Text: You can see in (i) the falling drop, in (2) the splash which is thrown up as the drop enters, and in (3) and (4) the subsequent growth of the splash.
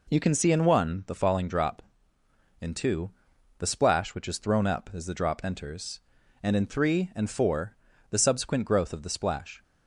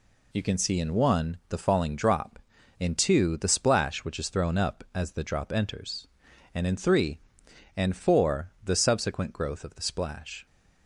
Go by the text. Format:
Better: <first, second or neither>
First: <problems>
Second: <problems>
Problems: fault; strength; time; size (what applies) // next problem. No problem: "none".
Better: neither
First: none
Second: none